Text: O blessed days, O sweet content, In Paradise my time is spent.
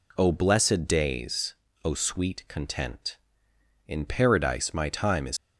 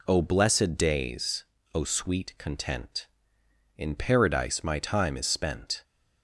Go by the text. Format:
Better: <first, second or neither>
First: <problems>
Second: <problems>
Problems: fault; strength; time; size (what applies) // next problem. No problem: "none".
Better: second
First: stops before "spent"; at 5.3 s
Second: none